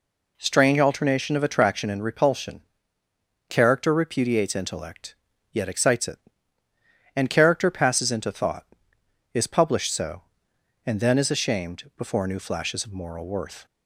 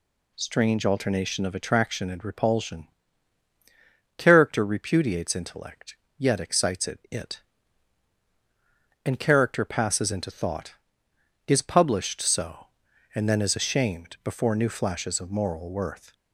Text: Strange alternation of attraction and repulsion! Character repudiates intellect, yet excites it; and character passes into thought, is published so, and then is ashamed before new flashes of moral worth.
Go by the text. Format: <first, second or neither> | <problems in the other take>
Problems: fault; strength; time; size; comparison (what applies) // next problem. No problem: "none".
first | says "it" twice; at 7.1 s